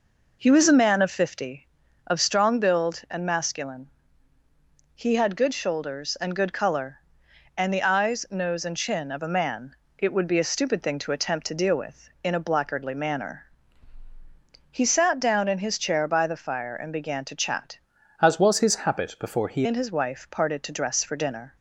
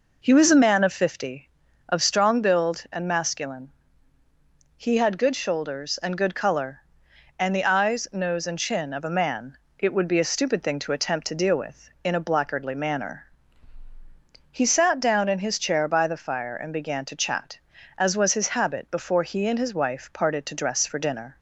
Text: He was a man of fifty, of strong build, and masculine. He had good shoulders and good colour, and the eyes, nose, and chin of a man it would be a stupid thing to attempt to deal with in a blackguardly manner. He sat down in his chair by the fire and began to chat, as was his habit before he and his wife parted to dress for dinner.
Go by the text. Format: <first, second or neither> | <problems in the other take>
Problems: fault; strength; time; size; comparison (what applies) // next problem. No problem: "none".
second | pauses between "man" and "it"; slight; at 9.7 s; 0.22 s long; slight in the second // changes voice from "as" to "he"; from 18.2 to 19.6 s; 1.4 s long